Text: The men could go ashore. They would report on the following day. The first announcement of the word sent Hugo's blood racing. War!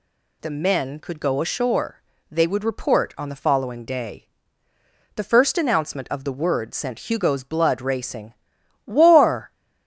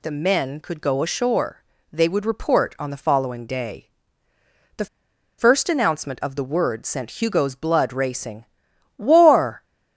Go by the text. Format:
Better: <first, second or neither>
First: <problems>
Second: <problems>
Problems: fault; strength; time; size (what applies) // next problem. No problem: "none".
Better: first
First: none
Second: pauses between "The" and "first"; noticeable; at 4.8 s; 0.52 s long